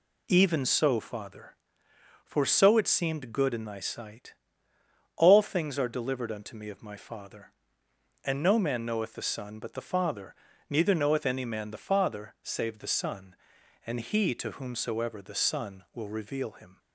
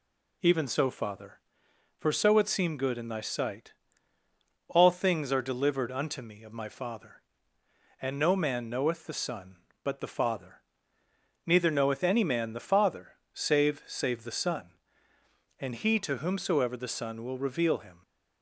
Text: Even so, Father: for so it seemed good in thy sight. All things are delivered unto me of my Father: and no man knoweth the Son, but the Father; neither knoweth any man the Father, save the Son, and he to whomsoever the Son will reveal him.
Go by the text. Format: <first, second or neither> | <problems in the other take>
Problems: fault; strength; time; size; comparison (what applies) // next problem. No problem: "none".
first | says "save" twice; at 13.8 s